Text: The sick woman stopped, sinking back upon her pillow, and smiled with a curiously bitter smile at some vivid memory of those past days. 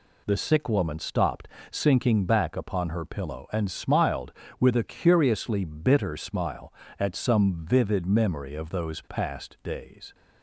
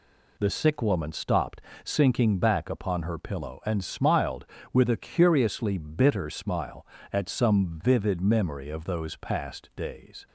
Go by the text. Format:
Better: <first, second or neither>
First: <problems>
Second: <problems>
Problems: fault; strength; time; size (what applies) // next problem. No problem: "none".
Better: neither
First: none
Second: none